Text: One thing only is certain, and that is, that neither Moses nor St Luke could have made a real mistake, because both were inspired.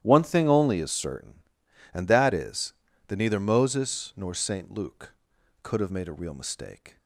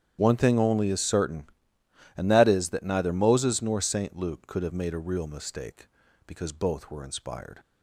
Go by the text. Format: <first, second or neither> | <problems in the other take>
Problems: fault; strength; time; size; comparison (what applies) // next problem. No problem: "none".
second | starts louder than the rest; strong; until 1.0 s; 12 dB; strong in the second // stops before "because both were inspired"; at 6.9 s